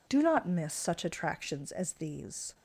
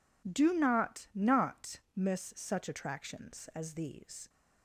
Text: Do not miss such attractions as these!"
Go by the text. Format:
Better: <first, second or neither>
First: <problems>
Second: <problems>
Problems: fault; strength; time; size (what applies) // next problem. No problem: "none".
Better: first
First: none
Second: says "not" twice; at 1.1 s